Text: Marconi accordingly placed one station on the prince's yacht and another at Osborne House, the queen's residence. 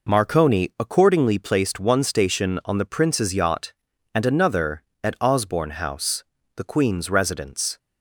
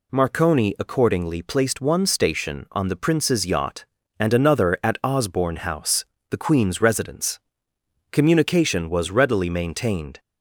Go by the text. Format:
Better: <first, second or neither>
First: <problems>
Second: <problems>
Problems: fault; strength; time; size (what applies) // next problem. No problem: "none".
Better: first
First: none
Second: goes on to say "Communication was readily maintained"; strong; from 8.0 s on; 2.1 s long